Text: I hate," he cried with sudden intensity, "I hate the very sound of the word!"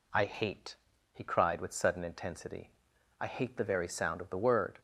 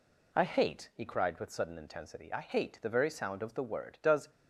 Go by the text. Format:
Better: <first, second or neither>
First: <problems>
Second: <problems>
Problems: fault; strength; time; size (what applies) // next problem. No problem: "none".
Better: first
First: none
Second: goes on to say "Does"; slight; from 4.0 s on; 0.30 s long